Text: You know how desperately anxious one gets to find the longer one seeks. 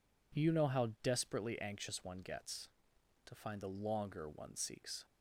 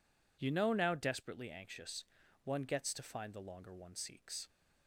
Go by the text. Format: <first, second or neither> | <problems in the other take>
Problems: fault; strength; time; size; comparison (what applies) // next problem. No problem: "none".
first | says "now" for "how"; at 0.7 s // pauses between "anxious" and "one"; at 2.0 s; 0.40 s long